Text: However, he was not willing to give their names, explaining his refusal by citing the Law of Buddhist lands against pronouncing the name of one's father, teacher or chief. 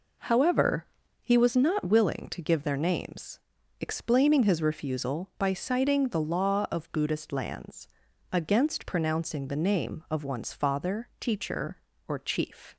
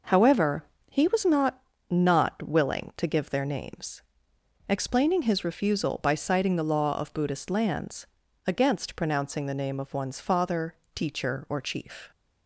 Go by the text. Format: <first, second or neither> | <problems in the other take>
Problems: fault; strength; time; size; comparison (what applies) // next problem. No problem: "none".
first | says "not" twice; at 1.8 s // pauses between "lands" and "against"; at 8.0 s; 0.40 s long; also in the first